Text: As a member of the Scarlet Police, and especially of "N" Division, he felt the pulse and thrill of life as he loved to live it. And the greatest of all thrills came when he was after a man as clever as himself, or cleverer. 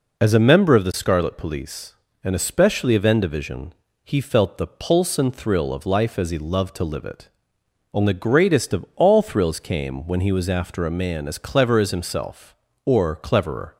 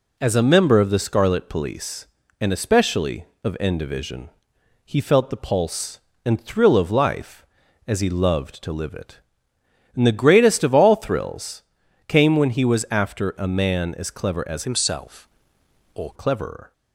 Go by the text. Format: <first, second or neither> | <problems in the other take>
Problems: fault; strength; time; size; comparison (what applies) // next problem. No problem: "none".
first | pauses between "thrills" and "came"; at 11.6 s; 0.44 s long // changes voice from "himself" to "or"; from 14.6 to 16.1 s; 1.5 s long